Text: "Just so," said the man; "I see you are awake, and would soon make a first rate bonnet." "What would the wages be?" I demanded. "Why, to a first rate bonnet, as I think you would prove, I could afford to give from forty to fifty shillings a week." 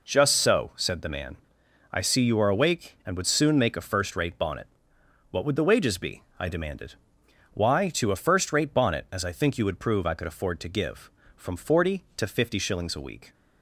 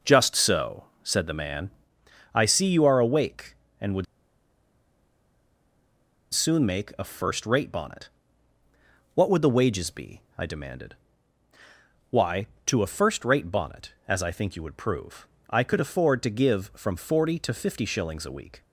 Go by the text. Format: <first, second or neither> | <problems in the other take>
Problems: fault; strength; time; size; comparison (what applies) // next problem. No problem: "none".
first | pauses between "would" and "soon"; strong; at 4.0 s; 2.2 s long